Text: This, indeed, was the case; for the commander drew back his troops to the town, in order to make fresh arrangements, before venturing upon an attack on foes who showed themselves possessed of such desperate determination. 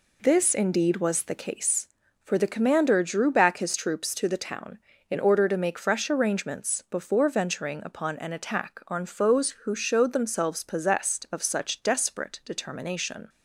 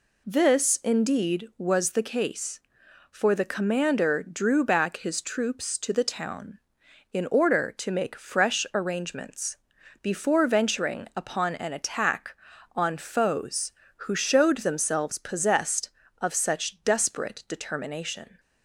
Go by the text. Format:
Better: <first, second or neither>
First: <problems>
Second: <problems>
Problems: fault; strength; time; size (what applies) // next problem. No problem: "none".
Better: neither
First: none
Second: none